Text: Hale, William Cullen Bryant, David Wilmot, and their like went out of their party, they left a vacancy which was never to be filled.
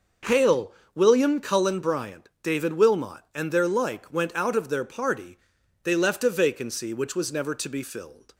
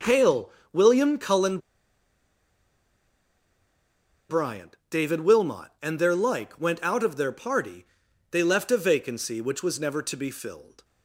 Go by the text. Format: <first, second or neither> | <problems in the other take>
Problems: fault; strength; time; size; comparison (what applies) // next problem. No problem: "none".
first | pauses between "Cullen" and "Bryant"; strong; at 1.5 s; 2.7 s long